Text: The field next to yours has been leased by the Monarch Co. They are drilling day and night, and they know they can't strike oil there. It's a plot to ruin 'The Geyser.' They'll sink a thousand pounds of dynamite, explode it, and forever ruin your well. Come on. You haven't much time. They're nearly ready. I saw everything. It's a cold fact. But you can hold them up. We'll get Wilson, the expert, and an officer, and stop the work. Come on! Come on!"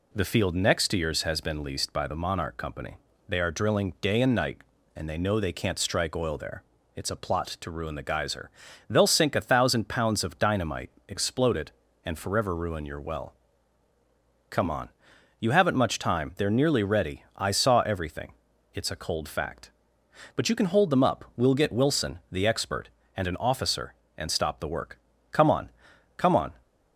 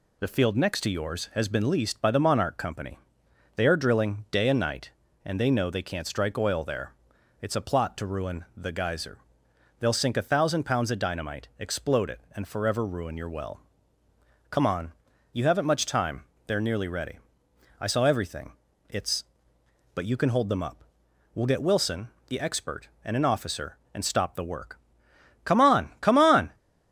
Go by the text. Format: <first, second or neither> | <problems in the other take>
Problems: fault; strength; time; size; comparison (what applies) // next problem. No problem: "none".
first | skips "a cold fact"; at 19.5 s